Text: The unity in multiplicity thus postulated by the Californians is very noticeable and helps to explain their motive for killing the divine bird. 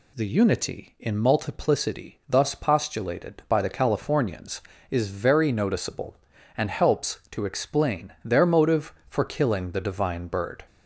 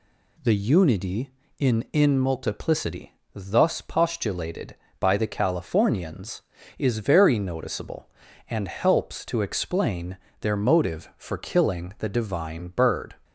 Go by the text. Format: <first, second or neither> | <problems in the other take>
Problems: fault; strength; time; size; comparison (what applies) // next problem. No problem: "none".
first | says "in" twice; at 1.9 s // pauses between "multiplicity" and "thus"; slight; at 3.1 s; 0.20 s long // pauses between "explain" and "their"; slight; at 10.1 s; 0.24 s long